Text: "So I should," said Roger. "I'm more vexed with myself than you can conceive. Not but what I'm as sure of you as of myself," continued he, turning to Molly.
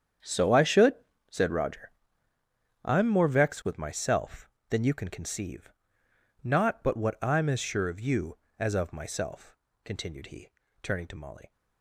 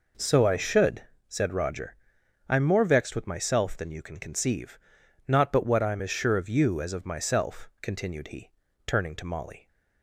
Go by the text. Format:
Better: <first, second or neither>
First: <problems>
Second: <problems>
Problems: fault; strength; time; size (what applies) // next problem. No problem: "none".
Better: second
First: gets quieter; strong; throughout; 15 dB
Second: none